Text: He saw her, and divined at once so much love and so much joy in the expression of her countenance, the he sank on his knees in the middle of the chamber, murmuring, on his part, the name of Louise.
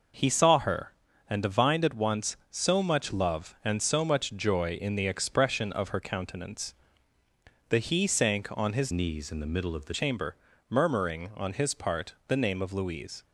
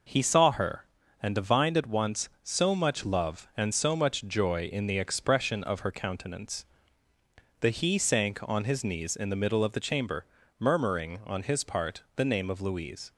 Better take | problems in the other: second | changes voice from "knees" to "the"; from 8.9 to 9.9 s; 1.0 s long

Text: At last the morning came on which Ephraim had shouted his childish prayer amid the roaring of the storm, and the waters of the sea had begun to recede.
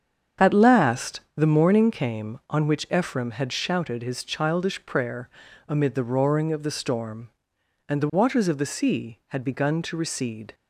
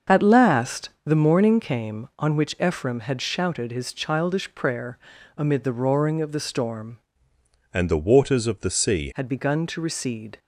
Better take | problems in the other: first | starts louder than the rest; until 1.2 s; 6.5 dB; strong in the first // pauses between "last" and "the"; slight; at 0.8 s; 0.16 s long; slight in the first // pauses between "prayer" and "amid"; at 4.9 s; 0.40 s long; also in the first // changes voice from "and" to "sea"; from 7.7 to 9.1 s; 1.4 s long

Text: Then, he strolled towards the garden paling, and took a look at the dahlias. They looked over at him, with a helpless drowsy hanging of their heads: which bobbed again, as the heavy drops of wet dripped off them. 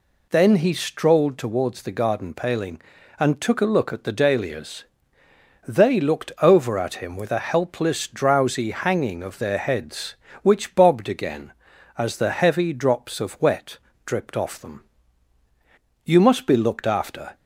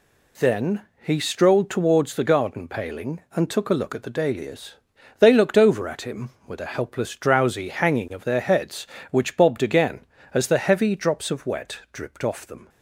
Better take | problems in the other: second | pauses between "wet" and "dripped"; slight; at 13.7 s; 0.28 s long // goes on to say "You must be looked after"; noticeable; from 16.0 s on; 1.3 s long

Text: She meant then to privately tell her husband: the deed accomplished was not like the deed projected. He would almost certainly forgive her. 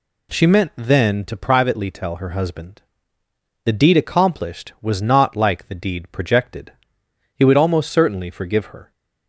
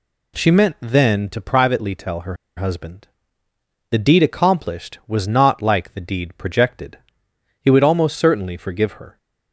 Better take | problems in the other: first | pauses between "her" and "husband"; slight; at 2.3 s; 0.22 s long

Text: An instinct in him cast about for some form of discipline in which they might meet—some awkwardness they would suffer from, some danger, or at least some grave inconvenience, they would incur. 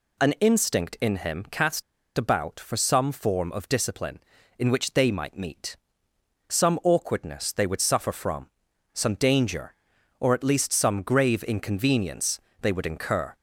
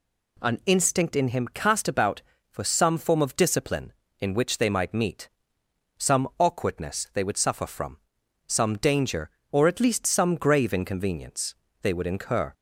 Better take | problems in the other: second | pauses between "cast" and "about"; slight; at 1.8 s; 0.34 s long

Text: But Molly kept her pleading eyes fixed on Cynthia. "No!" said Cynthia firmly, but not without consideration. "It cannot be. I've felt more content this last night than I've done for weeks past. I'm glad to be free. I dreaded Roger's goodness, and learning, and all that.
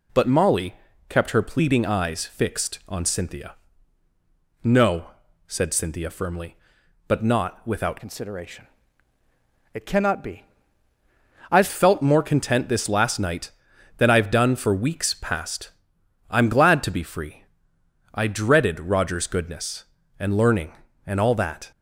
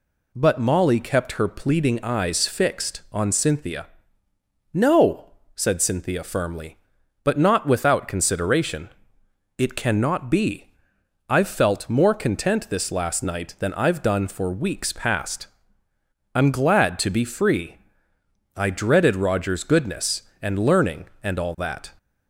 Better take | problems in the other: second | pauses between "Molly" and "kept"; slight; at 0.7 s; 0.34 s long // changes voice from "consideration" to "I've"; from 8.0 to 11.6 s; 3.6 s long

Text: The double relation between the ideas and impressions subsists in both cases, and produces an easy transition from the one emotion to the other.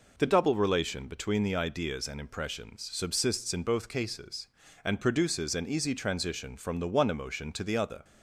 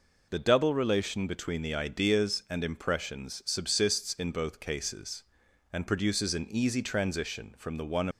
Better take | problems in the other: first | stops before "emotion to the other"; at 8.1 s

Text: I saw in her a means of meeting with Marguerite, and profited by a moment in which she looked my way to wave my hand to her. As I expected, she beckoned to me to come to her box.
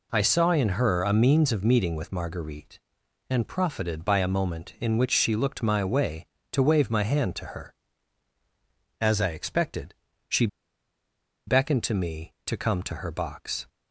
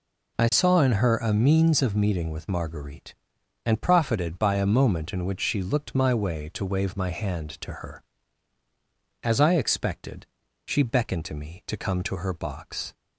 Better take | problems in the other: second | pauses between "she" and "beckoned"; at 10.4 s; 1.0 s long

